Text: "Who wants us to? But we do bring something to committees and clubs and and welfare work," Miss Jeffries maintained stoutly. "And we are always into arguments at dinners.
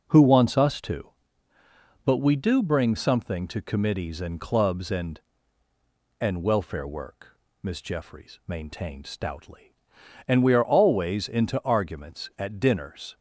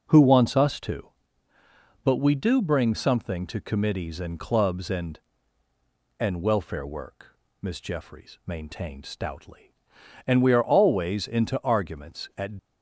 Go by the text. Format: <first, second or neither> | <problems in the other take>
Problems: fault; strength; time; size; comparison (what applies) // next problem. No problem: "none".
first | stops before "dinners"; at 12.5 s